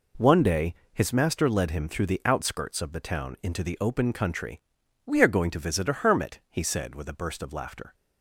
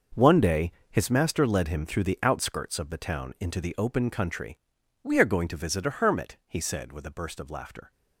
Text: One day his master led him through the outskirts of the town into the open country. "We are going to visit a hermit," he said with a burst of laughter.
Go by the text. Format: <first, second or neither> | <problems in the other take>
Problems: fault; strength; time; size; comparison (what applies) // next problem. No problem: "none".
first | gets quieter; strong; throughout; 12.5 dB // pauses between "day" and "his"; slight; at 0.7 s; 0.20 s long; slight in the first